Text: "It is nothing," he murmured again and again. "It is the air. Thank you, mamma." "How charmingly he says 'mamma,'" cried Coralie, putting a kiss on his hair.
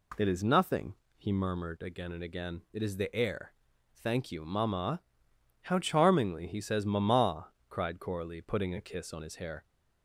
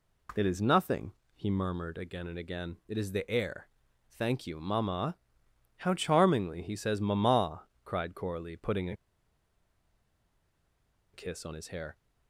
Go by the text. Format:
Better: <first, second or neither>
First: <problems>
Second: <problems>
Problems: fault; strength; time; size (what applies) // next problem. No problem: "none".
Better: first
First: none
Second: pauses between "a" and "kiss"; strong; at 8.9 s; 2.1 s long